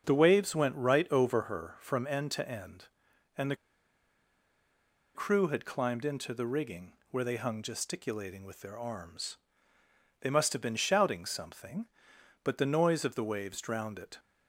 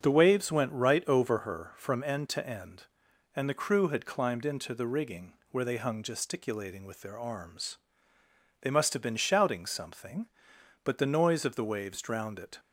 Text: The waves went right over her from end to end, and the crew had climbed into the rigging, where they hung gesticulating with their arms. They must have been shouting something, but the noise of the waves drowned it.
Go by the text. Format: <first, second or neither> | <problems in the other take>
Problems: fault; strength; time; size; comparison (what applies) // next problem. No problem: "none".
second | starts louder than the rest; until 1.0 s; 6.5 dB; also in the second // pauses between "the" and "crew"; strong; at 3.5 s; 1.5 s long